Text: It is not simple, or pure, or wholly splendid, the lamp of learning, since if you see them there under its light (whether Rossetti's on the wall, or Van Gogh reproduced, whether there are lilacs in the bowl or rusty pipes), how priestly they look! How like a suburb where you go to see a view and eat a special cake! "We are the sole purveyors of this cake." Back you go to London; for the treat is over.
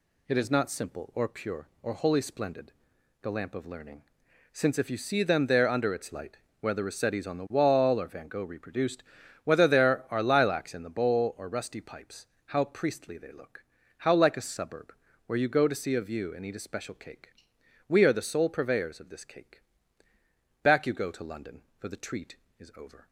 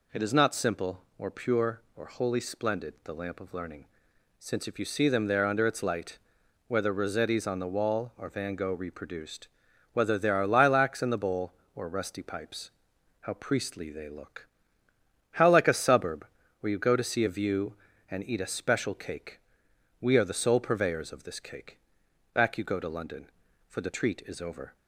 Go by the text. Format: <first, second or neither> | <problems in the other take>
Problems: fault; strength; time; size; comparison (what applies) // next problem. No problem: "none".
neither | pauses between "suburb" and "where"; the same in both